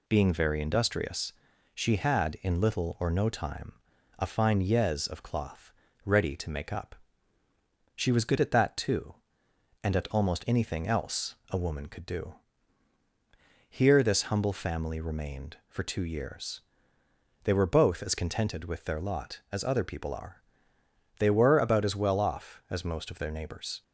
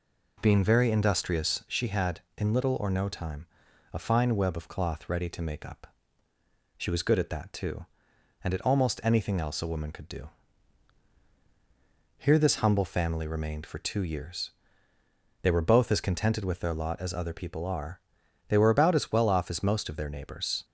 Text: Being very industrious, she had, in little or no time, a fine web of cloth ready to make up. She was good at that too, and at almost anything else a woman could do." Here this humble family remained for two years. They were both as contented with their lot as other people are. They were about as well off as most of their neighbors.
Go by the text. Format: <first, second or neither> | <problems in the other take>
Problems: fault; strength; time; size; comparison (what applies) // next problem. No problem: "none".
second | says "yez" for "web"; at 4.6 s // pauses between "cloth" and "ready"; slight; at 5.7 s; 0.32 s long // pauses between "else" and "a"; slight; at 11.3 s; 0.16 s long